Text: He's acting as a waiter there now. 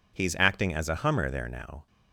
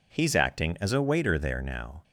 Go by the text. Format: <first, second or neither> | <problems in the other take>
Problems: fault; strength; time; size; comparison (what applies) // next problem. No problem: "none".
second | says "hummer" for "waiter"; at 0.9 s